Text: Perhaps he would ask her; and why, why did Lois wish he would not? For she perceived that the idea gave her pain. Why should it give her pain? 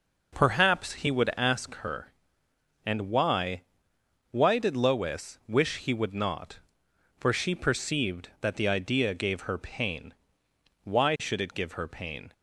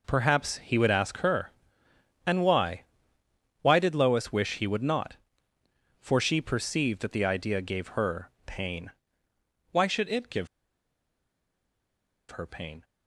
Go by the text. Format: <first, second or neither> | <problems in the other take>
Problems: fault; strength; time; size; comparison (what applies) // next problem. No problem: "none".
first | pauses between "give" and "her"; strong; at 10.4 s; 1.8 s long